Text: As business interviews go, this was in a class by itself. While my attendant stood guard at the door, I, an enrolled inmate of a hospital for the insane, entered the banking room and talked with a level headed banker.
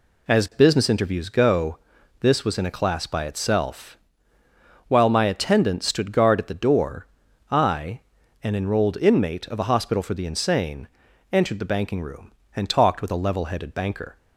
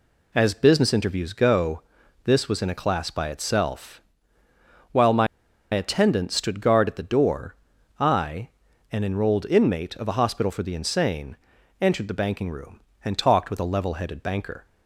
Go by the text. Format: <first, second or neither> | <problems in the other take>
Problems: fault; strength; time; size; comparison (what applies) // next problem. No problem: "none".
first | pauses between "my" and "attendant"; noticeable; at 5.2 s; 0.46 s long